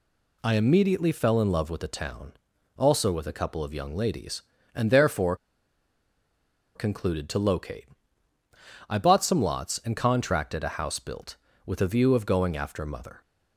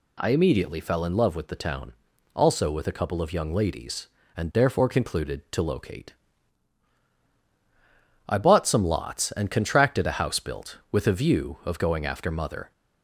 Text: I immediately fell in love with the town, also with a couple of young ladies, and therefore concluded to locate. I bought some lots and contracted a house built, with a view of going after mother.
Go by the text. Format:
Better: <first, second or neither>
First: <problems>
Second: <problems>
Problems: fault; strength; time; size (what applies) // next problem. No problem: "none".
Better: second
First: pauses between "therefore" and "concluded"; strong; at 5.3 s; 1.4 s long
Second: none